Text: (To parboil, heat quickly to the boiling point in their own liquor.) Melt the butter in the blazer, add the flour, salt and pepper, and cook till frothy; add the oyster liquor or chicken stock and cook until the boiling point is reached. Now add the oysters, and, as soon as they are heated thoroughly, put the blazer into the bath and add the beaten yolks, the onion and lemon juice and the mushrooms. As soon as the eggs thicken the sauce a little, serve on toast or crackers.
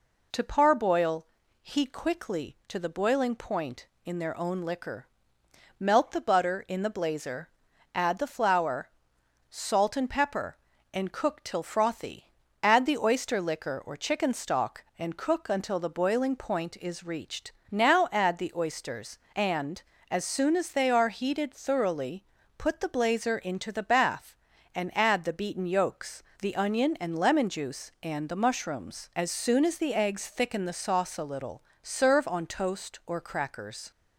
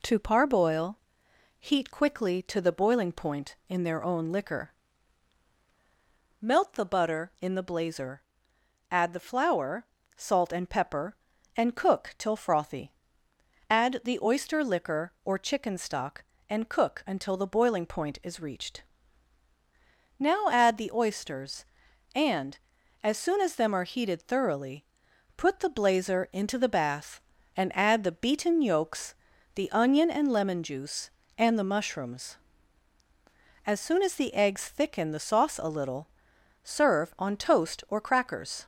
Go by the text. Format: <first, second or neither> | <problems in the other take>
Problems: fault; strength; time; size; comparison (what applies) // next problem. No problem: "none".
first | says "them" for "they"; at 23.5 s